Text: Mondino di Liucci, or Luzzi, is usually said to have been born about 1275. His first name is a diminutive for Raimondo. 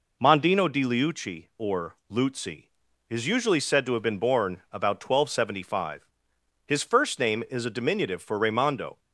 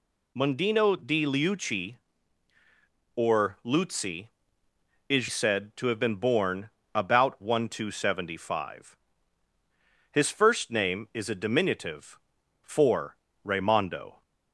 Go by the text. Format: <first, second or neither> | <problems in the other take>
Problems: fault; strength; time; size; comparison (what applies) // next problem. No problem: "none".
first | skips "usually"; at 5.2 s // pauses between "born" and "about"; slight; at 6.6 s; 0.24 s long // pauses between "for" and "Raimondo"; slight; at 13.1 s; 0.28 s long